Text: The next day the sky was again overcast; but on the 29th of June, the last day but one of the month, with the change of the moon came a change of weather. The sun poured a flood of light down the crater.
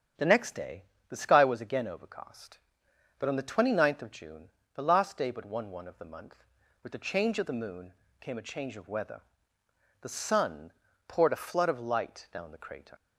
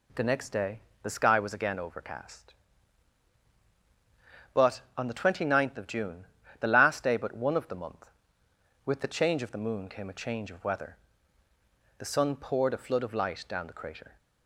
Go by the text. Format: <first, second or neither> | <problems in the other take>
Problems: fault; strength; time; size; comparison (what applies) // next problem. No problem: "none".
second | starts louder than the rest; strong; until 1.4 s; 8.5 dB // pauses between "day" and "the"; slight; at 0.8 s; 0.26 s long; slight in the second // says "one" twice; at 5.7 s // pauses between "moon" and "came"; slight; at 7.9 s; 0.28 s long // pauses between "sun" and "poured"; slight; at 10.7 s; 0.36 s long